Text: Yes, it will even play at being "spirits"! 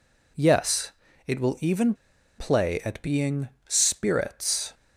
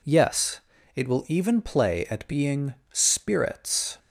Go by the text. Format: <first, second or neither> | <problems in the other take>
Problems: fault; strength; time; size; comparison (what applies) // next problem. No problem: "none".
second | pauses between "even" and "play"; at 1.9 s; 0.44 s long // pauses between "being" and "spirits"; slight; at 3.4 s; 0.18 s long; slight in the second